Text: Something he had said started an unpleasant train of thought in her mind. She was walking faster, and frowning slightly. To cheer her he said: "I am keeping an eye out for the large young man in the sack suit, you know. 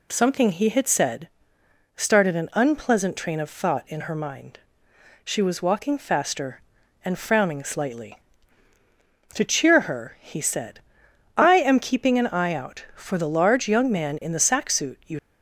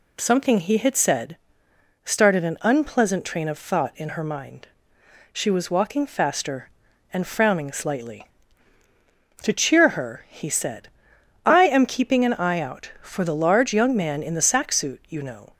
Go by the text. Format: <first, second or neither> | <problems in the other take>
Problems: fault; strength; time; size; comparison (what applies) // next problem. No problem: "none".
second | pauses between "said" and "started"; noticeable; at 1.2 s; 0.68 s long; noticeable in the second // stops before "know"; at 15.1 s